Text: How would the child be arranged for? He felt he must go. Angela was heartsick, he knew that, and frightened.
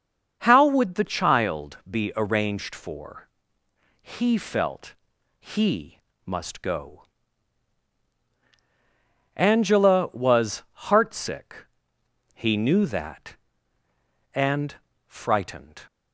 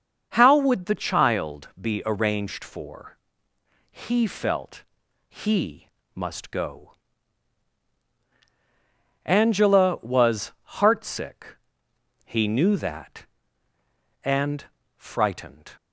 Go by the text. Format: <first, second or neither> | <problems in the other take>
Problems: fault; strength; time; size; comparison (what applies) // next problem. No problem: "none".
neither | starts louder than the rest; the same in both // pauses between "felt" and "he"; noticeable; the same in both // pauses between "he" and "must"; slight; the same in both // pauses between "was" and "heartsick"; slight; the same in both // pauses between "and" and "frightened"; slight; the same in both